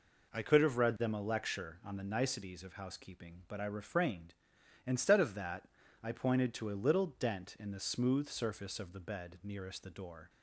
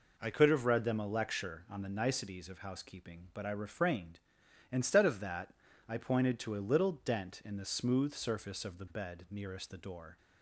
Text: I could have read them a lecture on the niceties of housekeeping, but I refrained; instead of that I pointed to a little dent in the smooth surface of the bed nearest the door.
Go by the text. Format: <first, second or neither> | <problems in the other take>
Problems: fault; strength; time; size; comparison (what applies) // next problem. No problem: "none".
neither | pauses between "that" and "I"; slight; the same in both